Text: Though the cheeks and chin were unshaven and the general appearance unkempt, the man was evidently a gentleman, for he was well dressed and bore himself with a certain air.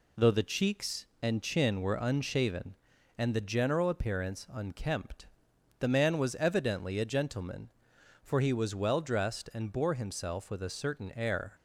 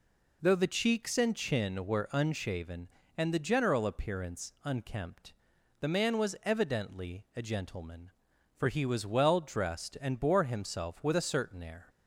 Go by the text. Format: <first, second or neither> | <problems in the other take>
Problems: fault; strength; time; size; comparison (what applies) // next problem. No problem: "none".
neither | none